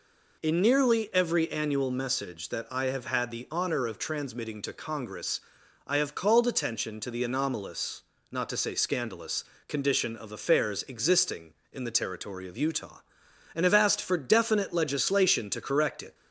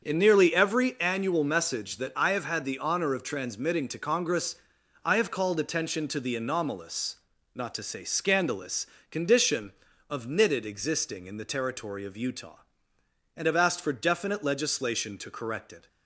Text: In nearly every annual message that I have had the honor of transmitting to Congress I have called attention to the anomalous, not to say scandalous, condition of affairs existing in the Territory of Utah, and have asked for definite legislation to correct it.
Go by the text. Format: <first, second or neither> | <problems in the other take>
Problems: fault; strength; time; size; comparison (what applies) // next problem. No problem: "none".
first | starts louder than the rest; until 1.0 s; 7 dB // pauses between "Congress" and "I"; noticeable; at 4.5 s; 0.50 s long; also in the first // says "knitted" for "affairs"; at 10.2 s